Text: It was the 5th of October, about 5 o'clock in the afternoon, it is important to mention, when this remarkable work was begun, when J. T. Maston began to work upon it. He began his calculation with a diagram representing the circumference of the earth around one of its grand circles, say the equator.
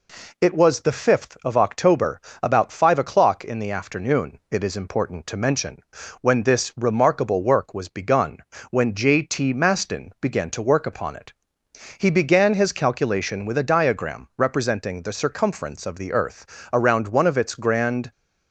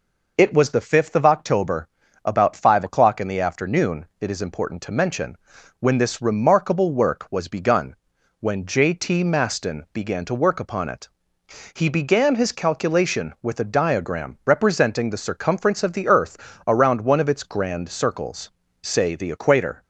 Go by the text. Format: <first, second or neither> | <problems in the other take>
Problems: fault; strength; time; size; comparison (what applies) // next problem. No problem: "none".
second | pauses between "earth" and "around"; slight; at 16.4 s; 0.28 s long; slight in the second // stops before "circles say the equator"; at 18.1 s